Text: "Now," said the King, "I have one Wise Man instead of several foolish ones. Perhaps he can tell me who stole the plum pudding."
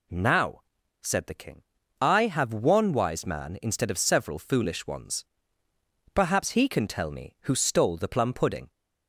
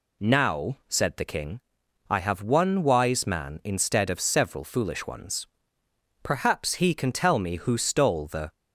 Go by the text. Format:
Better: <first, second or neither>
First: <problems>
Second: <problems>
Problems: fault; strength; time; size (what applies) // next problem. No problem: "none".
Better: first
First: none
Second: stops before "plum pudding"; at 8.5 s